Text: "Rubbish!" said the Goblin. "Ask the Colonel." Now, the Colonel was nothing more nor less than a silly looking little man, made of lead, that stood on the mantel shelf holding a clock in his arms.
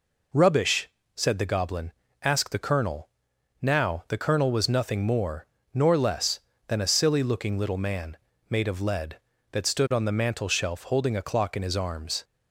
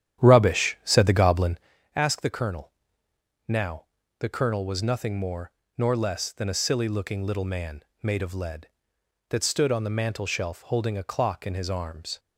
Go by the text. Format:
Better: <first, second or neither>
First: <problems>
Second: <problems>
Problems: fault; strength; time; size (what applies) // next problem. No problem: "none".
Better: first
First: pauses between "more" and "nor"; slight; at 5.4 s; 0.26 s long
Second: starts louder than the rest; strong; until 1.7 s; 10 dB // pauses between "more" and "nor"; slight; at 5.5 s; 0.26 s long